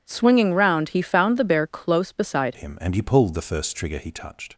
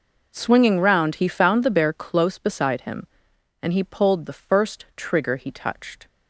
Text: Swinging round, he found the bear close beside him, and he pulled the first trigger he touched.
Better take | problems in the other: second | changes voice at "him"; from 2.5 s on; 2.0 s long

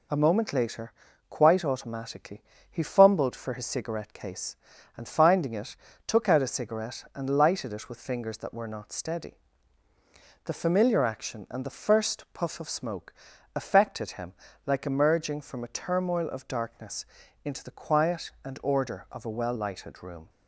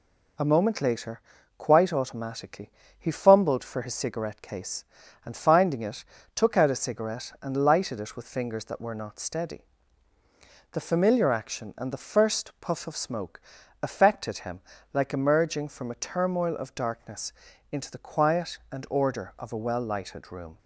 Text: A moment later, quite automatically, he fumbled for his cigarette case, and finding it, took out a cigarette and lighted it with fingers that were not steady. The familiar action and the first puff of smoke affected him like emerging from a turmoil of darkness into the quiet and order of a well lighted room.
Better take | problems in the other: neither | pauses between "smoke" and "affected"; the same in both // pauses between "him" and "like"; slight; the same in both // pauses between "darkness" and "into"; the same in both

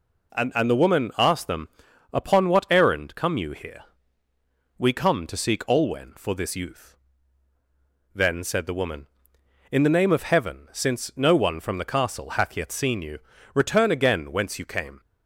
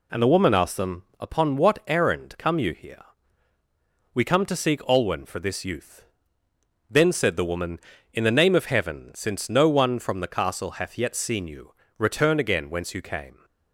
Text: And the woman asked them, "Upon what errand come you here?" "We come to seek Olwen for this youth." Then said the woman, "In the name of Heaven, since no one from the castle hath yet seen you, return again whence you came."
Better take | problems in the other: second | says "And" twice; at 0.5 s

